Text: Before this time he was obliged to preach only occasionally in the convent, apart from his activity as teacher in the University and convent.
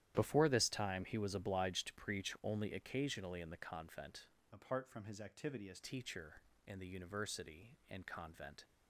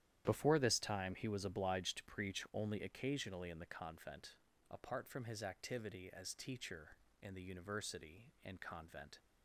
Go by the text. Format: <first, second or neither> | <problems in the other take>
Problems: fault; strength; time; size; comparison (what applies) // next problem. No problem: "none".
second | starts louder than the rest; strong; until 1.1 s; 11.5 dB; strong in the second // changes voice from "apart" to "as"; from 4.5 to 5.7 s; 1.2 s long